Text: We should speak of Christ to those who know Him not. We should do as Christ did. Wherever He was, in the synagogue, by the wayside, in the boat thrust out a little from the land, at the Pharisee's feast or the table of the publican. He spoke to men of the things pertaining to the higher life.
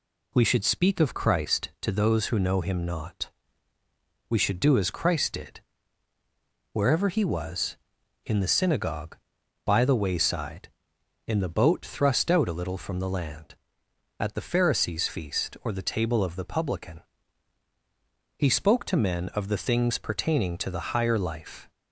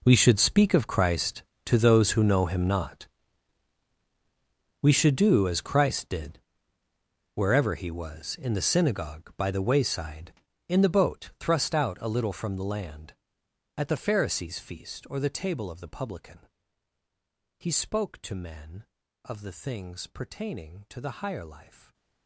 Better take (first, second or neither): first